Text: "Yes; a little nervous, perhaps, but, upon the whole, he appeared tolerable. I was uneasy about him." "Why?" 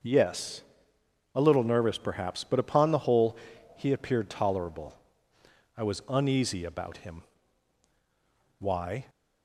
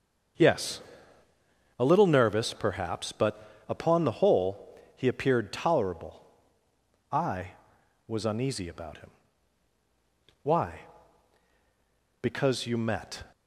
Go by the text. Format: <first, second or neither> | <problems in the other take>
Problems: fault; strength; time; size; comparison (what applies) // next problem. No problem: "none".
first | starts louder than the rest; until 2.3 s; 7 dB; noticeable in the first // goes on to say "Because you met"; noticeable; from 12.2 s on; 1.0 s long